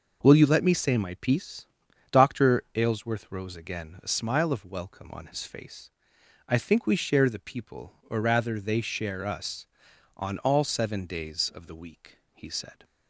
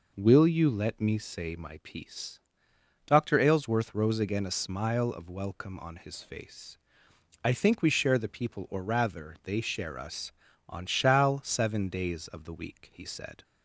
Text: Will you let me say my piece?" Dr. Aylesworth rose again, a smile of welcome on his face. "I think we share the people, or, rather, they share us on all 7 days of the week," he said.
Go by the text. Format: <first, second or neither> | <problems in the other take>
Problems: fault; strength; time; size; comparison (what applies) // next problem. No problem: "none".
first | says "shall" for "all"; at 10.8 s